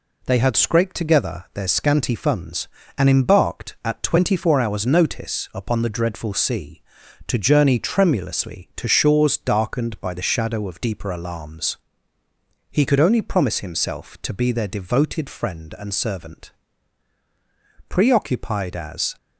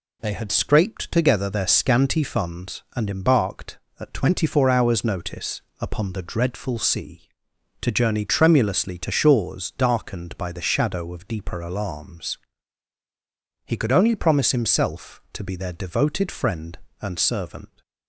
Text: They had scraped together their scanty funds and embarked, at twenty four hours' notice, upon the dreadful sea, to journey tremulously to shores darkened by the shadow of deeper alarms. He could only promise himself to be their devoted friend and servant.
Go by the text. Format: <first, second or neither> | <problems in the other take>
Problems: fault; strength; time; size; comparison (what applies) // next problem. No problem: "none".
second | goes on to say "Preoccupied as"; noticeable; from 17.8 s on; 1.2 s long